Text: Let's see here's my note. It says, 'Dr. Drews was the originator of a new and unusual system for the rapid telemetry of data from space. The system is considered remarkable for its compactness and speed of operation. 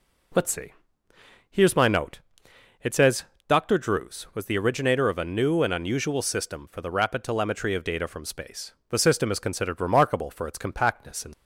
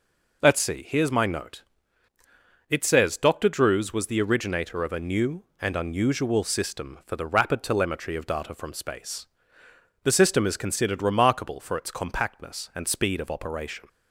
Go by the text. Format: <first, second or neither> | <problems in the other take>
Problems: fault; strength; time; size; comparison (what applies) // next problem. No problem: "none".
second | pauses between "see" and "here's"; noticeable; at 0.7 s; 0.76 s long // stops before "speed of operation"; at 11.3 s